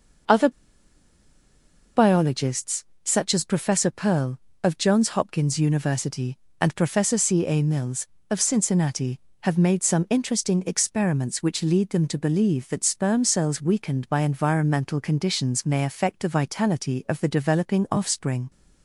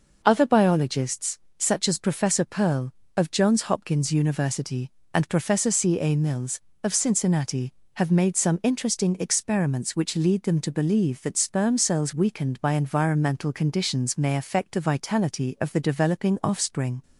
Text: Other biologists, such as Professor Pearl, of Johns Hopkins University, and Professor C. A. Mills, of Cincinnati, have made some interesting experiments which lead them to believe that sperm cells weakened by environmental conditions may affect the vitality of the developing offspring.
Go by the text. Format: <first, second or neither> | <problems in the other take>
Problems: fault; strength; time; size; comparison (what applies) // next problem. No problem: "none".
second | pauses between "Other" and "biologists"; strong; at 0.4 s; 1.4 s long